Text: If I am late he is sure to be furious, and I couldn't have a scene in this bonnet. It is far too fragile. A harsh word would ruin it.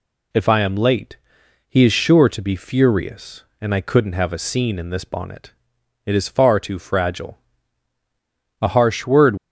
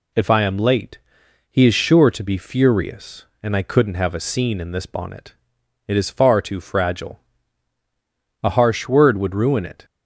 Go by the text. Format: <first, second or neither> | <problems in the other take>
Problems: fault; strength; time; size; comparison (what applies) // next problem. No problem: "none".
second | pauses between "late" and "he"; noticeable; at 1.1 s; 0.50 s long; noticeable in the second // stops before "would ruin it"; at 9.3 s